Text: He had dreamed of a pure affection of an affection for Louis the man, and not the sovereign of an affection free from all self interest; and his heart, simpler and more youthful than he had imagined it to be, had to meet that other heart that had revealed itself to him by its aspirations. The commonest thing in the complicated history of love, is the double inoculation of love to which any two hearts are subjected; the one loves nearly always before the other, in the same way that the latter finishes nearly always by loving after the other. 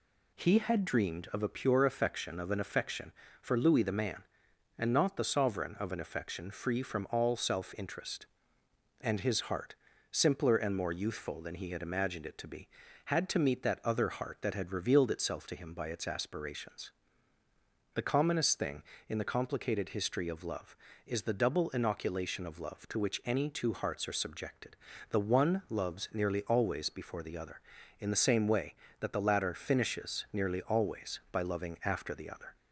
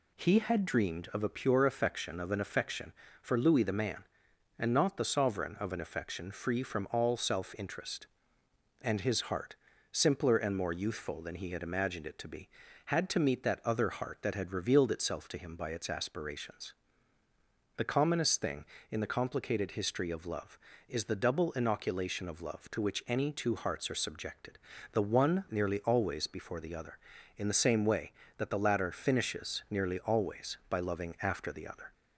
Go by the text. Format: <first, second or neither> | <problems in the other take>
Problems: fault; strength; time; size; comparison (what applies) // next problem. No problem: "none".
first | skips "loves"; at 25.4 s